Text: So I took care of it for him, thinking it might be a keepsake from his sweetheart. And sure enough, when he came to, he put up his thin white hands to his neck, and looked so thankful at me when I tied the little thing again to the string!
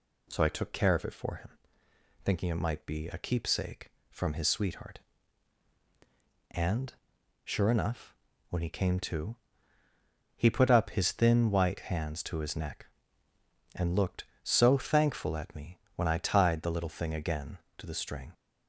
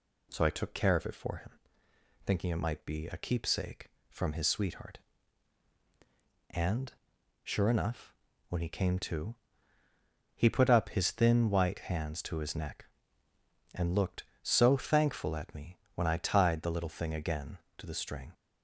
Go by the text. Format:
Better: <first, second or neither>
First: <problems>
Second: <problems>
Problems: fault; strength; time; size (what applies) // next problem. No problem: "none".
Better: neither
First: pauses between "And" and "sure"; noticeable; at 6.9 s; 0.52 s long // pauses between "me" and "when"; slight; at 15.7 s; 0.16 s long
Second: pauses between "And" and "sure"; noticeable; at 6.9 s; 0.52 s long // pauses between "me" and "when"; slight; at 15.7 s; 0.16 s long